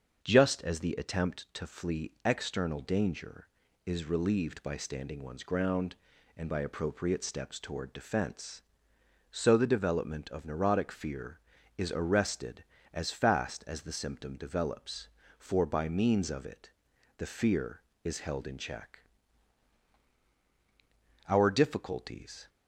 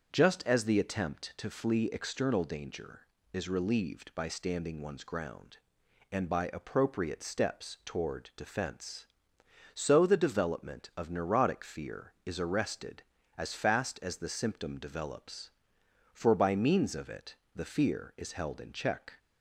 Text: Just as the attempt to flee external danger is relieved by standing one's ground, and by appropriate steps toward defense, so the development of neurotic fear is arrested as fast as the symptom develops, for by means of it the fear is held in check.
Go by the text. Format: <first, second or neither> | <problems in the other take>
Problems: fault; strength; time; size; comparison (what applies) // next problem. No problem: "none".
second | starts louder than the rest; until 1.2 s; 6.5 dB; also in the second // pauses between "it" and "the"; noticeable; at 16.7 s; 0.46 s long; slight in the second // goes on to say "Our difficulties"; noticeable; from 21.2 s on; 1.2 s long